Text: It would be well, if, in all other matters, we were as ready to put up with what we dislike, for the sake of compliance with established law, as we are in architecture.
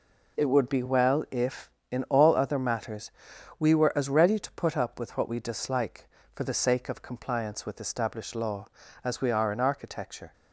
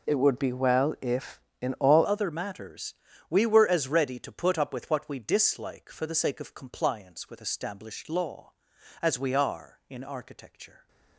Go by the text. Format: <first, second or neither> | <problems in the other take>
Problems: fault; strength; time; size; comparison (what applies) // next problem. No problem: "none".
first | changes voice at "other"; from 2.0 s on; 8.8 s long